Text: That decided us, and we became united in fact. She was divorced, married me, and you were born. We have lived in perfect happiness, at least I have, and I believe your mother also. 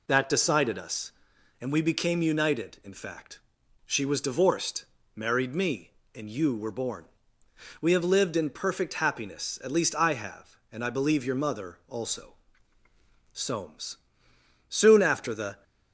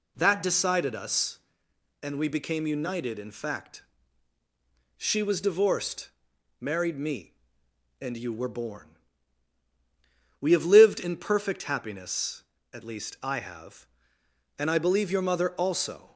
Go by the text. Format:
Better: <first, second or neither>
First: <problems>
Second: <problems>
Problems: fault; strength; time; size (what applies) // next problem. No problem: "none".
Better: second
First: goes on to say "Soames soon after the"; strong; from 13.3 s on; 2.3 s long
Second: none